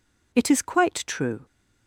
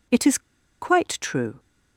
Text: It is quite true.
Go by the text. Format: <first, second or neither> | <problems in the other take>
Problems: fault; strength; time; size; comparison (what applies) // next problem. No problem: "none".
first | pauses between "is" and "quite"; at 0.3 s; 0.42 s long